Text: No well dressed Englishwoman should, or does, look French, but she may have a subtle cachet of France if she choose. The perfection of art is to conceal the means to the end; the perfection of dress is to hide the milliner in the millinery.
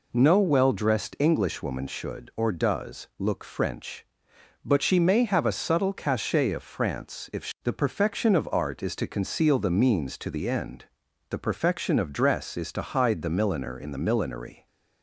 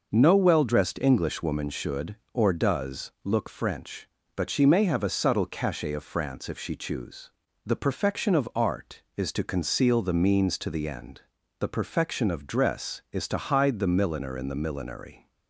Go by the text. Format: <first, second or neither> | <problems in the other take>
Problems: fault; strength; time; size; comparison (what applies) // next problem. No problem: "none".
second | skips "choose"; at 7.5 s